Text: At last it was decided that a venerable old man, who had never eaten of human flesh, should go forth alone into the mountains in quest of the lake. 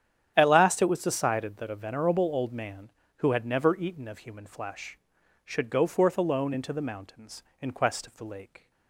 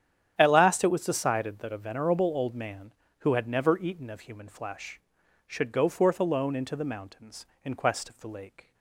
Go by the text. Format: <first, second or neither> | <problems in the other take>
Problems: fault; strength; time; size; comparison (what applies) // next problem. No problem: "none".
neither | starts louder than the rest; strong; the same in both